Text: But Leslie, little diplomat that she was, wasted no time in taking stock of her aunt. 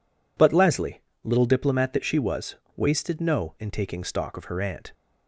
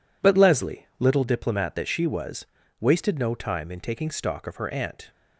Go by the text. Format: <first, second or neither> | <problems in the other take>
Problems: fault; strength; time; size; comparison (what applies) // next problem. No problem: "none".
second | skips "time"; at 3.5 s